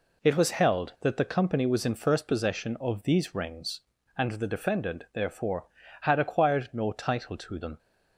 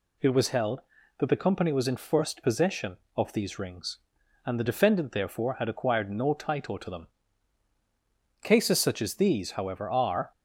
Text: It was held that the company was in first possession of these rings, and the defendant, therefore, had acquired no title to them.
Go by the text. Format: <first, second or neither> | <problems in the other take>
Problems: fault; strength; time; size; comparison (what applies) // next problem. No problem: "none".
first | goes on to say "Cases such as these however are"; strong; from 8.4 s on; 1.8 s long